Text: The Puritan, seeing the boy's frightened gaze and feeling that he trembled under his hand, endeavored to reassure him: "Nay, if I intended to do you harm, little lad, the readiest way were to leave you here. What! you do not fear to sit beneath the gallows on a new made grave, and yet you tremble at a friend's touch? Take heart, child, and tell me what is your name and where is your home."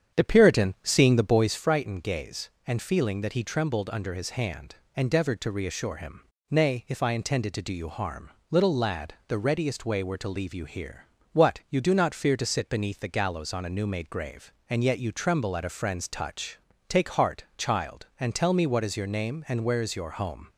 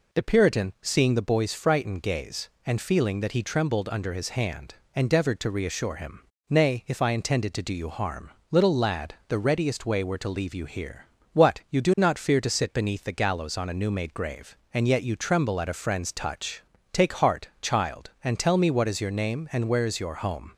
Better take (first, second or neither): second